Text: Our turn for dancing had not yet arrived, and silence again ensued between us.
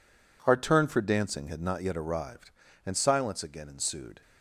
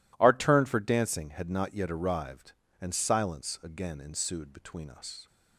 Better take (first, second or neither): second